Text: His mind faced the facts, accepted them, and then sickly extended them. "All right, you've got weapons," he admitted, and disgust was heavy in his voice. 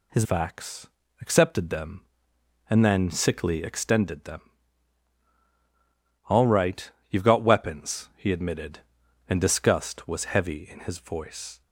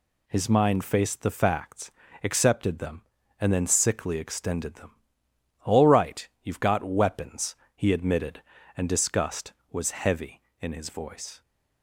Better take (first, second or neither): second